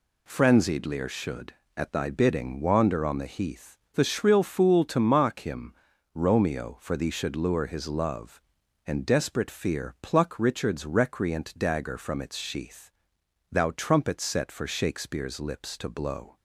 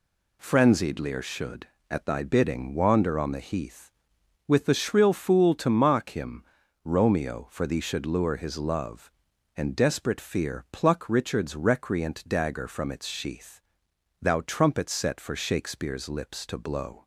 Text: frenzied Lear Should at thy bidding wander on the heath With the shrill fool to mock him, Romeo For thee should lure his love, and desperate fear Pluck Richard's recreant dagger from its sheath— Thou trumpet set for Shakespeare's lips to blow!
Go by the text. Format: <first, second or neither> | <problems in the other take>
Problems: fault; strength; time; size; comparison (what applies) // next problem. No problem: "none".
second | skips "With"; at 3.8 s